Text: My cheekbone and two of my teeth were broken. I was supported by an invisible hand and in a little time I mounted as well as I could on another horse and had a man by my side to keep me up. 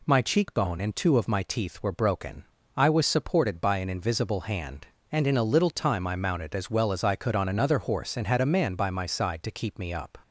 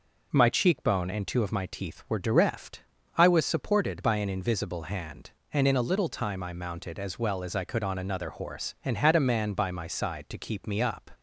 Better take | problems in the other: first | says "direft" for "broken"; at 2.2 s

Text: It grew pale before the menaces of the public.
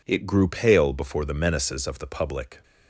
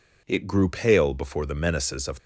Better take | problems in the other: first | stops before "the public"; at 2.1 s

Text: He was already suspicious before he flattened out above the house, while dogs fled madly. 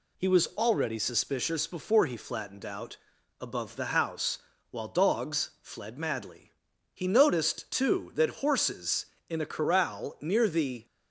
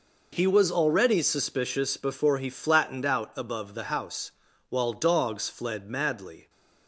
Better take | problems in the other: second | pauses between "out" and "above"; at 2.9 s; 0.44 s long // goes on to say "He noticed too that horses in a corral near the"; strong; from 6.9 s on; 3.9 s long

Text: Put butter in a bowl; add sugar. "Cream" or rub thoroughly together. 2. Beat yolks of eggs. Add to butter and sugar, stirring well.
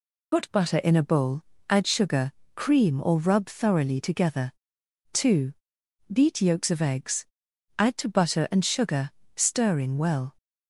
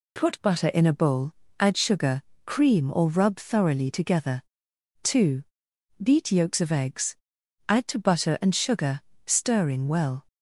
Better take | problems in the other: second | loses the start of "Put"; at 0.3 s; 65 ms

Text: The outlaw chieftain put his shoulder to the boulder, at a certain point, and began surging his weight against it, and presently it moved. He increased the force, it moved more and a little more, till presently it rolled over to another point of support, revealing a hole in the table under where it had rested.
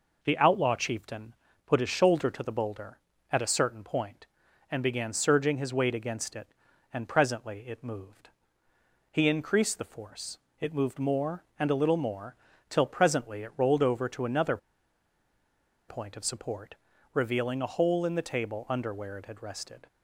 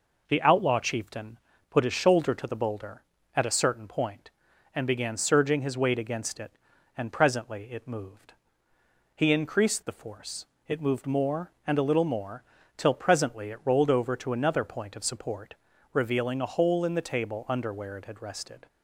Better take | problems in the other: second | pauses between "chieftain" and "put"; slight; at 1.3 s; 0.30 s long; slight in the second // pauses between "another" and "point"; strong; at 14.5 s; 1.3 s long

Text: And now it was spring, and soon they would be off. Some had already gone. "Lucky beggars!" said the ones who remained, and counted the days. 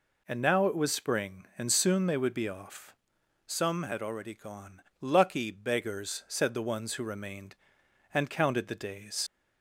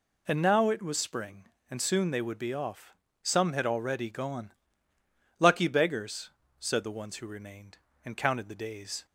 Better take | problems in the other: second | leaves "days" unfinished; at 9.2 s; 70 ms

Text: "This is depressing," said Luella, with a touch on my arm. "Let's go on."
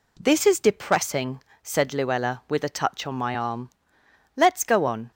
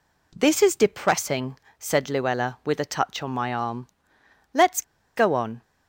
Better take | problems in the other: first | pauses between "Let's" and "go"; slight; at 4.8 s; 0.34 s long

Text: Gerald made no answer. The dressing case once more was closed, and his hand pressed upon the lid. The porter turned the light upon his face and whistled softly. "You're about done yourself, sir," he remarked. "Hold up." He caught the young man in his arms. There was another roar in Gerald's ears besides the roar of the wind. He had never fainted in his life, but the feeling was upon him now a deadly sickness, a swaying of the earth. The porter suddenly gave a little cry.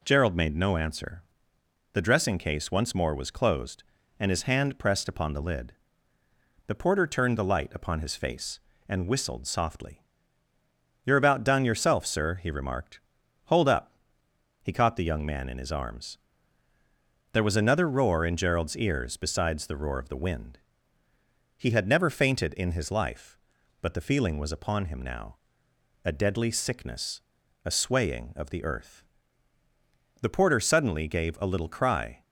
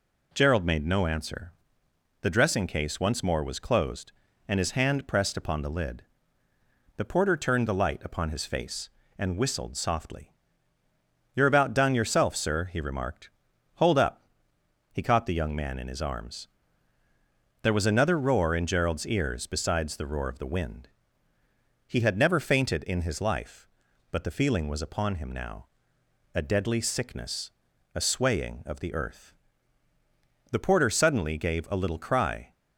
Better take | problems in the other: neither | pauses between "now" and "a"; noticeable; the same in both

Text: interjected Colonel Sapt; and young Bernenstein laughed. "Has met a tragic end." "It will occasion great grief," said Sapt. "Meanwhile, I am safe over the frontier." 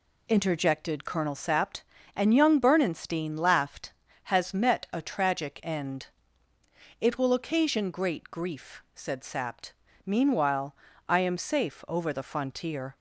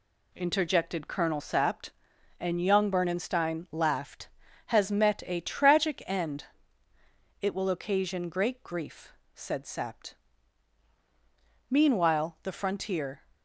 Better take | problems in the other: first | skips "I am safe over"; at 12.4 s

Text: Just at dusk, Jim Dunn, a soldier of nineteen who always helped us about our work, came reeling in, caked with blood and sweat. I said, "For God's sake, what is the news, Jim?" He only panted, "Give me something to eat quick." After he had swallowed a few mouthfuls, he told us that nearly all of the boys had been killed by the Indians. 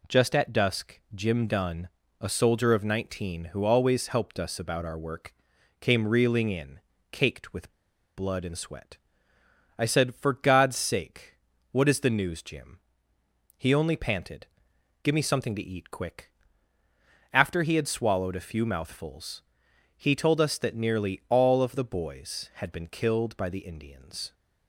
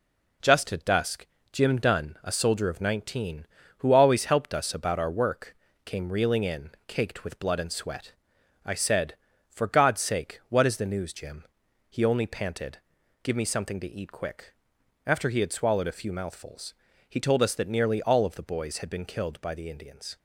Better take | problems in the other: second | pauses between "with" and "blood"; at 7.7 s; 0.41 s long

